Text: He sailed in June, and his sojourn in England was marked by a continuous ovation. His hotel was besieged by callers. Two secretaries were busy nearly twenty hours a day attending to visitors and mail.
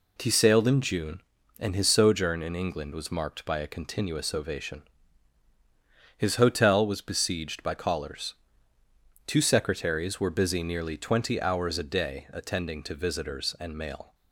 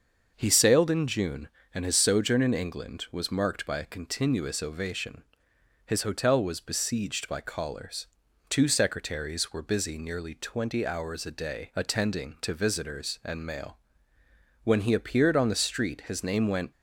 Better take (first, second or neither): first